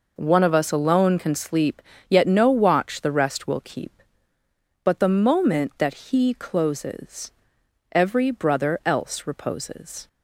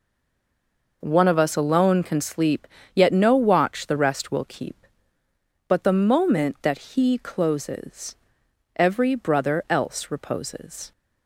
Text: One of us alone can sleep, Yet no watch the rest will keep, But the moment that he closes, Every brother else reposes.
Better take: first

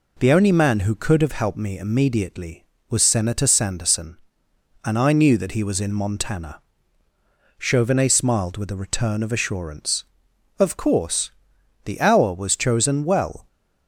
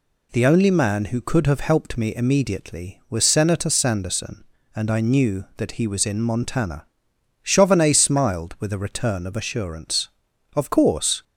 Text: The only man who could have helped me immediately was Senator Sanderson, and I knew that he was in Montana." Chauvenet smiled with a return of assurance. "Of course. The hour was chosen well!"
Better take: first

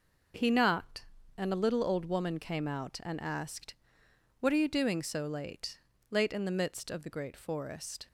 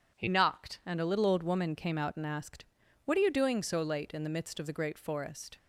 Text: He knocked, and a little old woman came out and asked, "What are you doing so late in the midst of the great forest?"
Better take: second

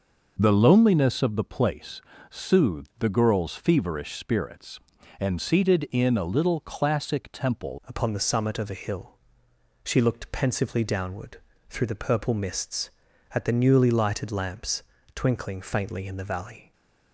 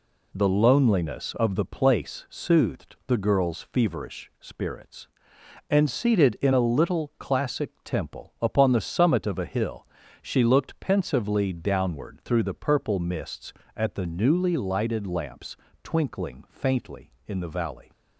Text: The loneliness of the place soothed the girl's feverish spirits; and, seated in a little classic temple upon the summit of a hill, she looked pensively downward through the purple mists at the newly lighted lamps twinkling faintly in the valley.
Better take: second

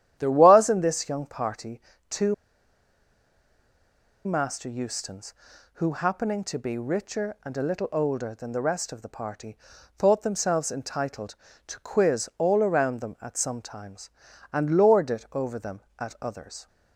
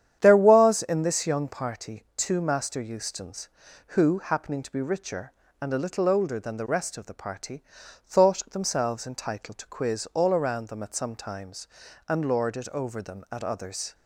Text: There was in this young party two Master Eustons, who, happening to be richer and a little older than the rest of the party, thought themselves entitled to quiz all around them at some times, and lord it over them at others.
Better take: second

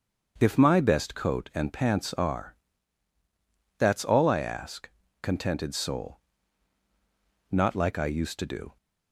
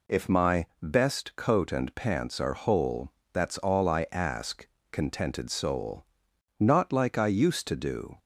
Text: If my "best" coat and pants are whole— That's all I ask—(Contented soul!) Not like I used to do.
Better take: second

